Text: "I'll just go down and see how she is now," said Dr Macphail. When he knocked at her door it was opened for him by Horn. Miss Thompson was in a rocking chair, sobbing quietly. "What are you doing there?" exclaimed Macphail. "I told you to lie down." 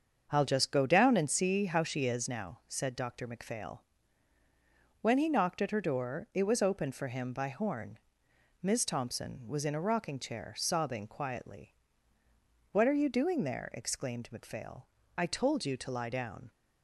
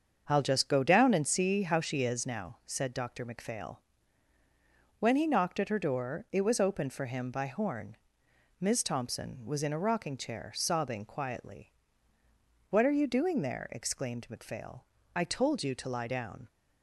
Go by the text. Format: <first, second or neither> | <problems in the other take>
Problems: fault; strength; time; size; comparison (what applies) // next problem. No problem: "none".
neither | starts louder than the rest; the same in both